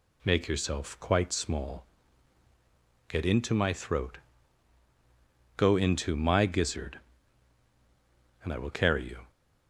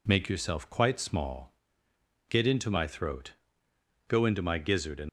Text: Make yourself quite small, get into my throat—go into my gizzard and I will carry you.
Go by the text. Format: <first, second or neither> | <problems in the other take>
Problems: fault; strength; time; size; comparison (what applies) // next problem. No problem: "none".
first | stops before "I will carry you"; at 5.0 s